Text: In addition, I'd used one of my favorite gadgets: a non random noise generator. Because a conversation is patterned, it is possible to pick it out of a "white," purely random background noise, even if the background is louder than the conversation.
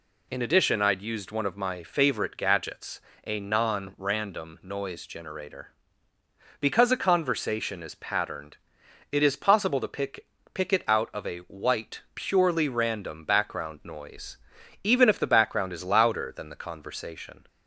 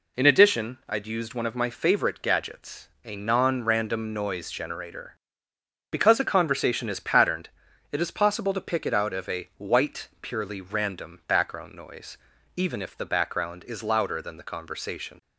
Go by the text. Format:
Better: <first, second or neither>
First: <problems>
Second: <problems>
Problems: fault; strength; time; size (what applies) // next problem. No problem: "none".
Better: second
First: says "pick" twice; at 10.5 s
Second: none